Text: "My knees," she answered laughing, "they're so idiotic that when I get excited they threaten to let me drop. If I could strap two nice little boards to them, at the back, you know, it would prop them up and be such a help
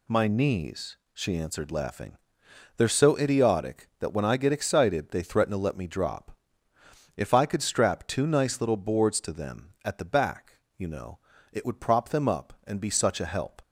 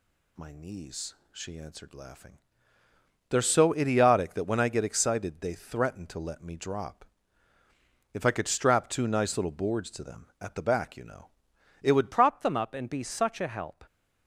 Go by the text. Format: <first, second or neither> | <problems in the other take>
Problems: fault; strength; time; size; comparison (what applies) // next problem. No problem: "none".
first | changes voice at "prop"; from 12.1 s on; 1.7 s long